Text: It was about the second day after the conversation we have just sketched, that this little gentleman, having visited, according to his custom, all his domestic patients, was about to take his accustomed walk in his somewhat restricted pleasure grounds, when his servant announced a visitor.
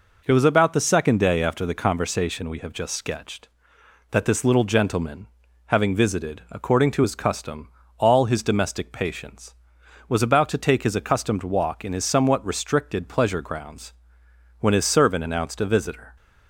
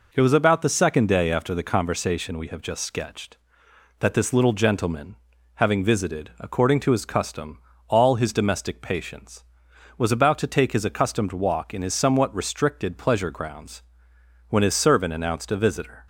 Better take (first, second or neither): neither